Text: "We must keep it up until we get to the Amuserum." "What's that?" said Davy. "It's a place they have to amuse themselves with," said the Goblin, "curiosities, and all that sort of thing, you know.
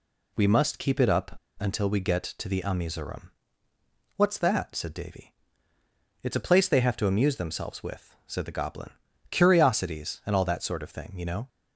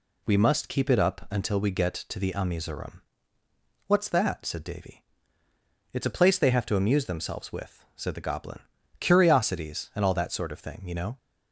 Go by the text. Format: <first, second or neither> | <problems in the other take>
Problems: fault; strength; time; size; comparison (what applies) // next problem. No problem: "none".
second | pauses between "up" and "until"; slight; at 1.3 s; 0.23 s long